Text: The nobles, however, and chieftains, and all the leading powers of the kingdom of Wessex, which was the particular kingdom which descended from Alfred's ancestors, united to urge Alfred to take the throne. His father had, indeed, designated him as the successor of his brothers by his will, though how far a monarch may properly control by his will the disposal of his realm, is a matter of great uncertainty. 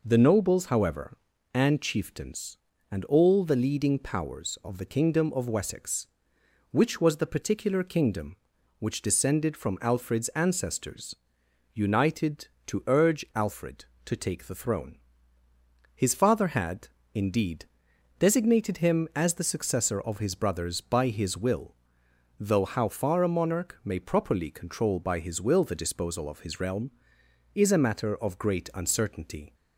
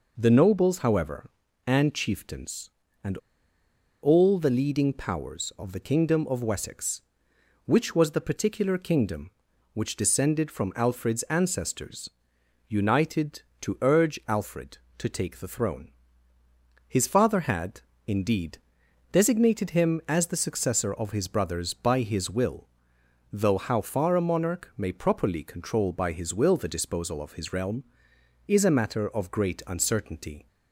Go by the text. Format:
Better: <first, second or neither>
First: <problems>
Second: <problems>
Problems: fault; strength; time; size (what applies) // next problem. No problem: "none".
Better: first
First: none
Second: pauses between "and" and "all"; noticeable; at 3.1 s; 0.84 s long